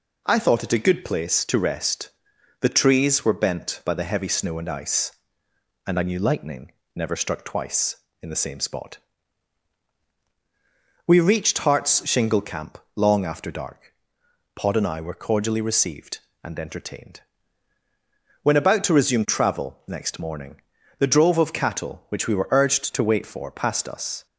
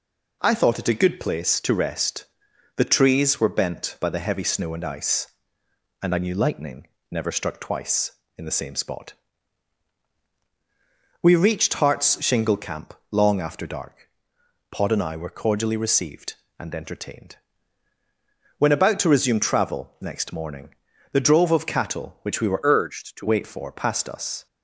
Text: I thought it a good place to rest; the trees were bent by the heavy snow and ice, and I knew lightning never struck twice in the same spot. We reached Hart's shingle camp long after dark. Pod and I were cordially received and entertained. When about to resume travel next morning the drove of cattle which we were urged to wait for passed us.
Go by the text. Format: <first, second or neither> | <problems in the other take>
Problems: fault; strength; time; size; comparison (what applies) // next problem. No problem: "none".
first | pauses between "lightning" and "never"; slight; at 6.8 s; 0.24 s long; slight in the first // pauses between "camp" and "long"; slight; at 12.9 s; 0.18 s long; slight in the first // pauses between "morning" and "the"; at 20.6 s; 0.42 s long; also in the first // changes voice from "urged" to "to"; from 22.6 to 23.2 s; 0.6 s long